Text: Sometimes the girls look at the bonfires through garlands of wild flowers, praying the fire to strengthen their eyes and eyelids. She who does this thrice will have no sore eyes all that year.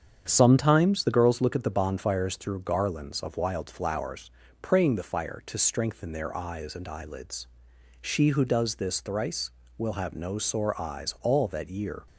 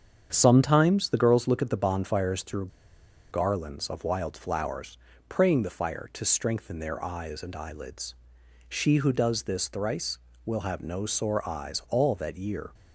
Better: first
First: starts louder than the rest; strong; until 1.2 s; 8 dB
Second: starts louder than the rest; strong; until 1.3 s; 8 dB // pauses between "through" and "garlands"; noticeable; at 2.6 s; 0.63 s long

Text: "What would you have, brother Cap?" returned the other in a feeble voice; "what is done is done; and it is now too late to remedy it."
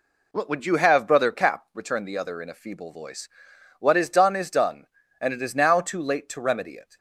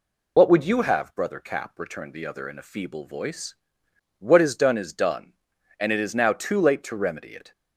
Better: first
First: none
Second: loses the start of "What"; at 0.3 s; 50 ms

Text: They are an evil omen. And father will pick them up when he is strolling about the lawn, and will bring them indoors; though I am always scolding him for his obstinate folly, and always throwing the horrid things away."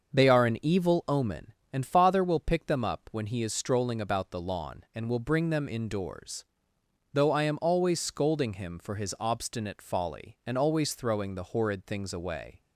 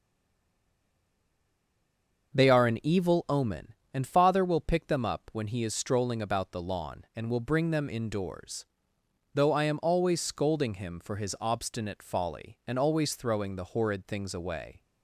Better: first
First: starts louder than the rest; until 1.2 s; 6.5 dB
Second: stays silent before the first word; until 2.3 s; 2.3 s long // starts louder than the rest; until 3.4 s; 6.5 dB

